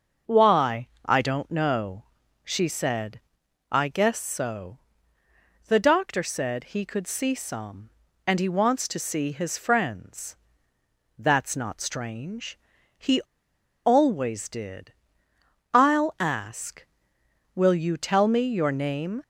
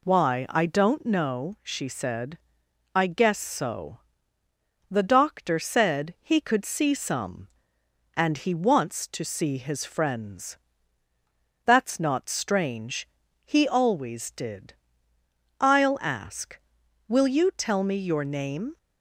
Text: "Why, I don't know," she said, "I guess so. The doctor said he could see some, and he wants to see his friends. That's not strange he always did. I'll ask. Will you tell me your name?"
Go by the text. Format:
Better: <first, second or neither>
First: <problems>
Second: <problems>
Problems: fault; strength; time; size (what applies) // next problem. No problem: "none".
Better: second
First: starts louder than the rest; noticeable; until 1.4 s; 6 dB // pauses between "strange" and "he"; at 12.5 s; 0.40 s long // pauses between "he" and "always"; noticeable; at 13.2 s; 0.66 s long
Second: pauses between "strange" and "he"; slight; at 13.0 s; 0.36 s long